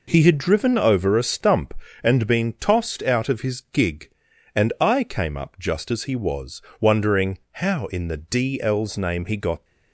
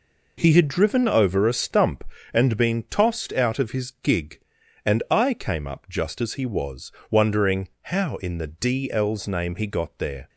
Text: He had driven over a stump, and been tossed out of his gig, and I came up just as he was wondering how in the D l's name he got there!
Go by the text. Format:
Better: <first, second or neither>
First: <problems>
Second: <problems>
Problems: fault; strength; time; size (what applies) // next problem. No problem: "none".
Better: second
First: pauses between "was" and "wondering"; slight; at 6.6 s; 0.18 s long // stops before "there"; at 9.6 s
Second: pauses between "was" and "wondering"; slight; at 6.9 s; 0.18 s long